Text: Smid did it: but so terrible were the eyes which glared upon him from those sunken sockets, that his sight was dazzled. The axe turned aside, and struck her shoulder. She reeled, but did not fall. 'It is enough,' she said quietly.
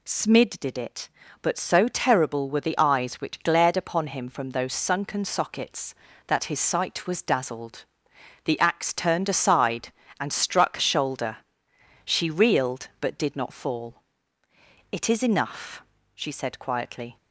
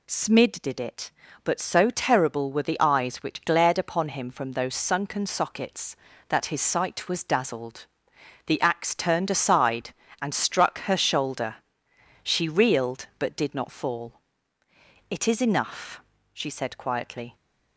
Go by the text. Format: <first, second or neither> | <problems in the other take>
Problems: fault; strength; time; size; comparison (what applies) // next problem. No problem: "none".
second | skips "her"; at 10.7 s